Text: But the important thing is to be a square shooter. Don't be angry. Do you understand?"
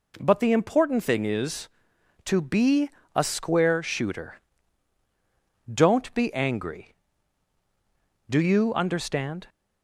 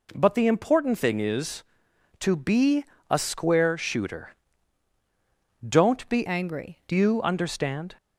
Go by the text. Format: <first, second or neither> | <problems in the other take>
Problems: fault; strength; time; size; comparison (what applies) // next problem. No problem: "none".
first | pauses between "be" and "a"; slight; at 2.8 s; 0.26 s long; slight in the first // changes voice from "angry" to "Do"; from 6.2 to 6.9 s; 0.7 s long